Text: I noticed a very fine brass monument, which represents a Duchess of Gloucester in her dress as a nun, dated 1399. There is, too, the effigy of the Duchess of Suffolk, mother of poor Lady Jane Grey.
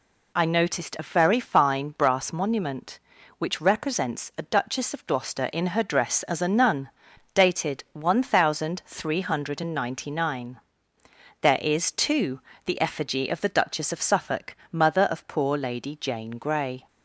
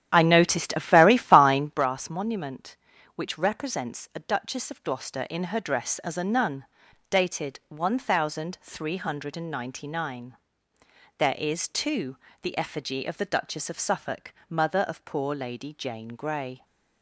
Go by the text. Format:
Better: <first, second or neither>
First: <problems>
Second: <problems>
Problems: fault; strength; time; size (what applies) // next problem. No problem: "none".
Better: first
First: none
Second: starts louder than the rest; strong; until 1.8 s; 10.5 dB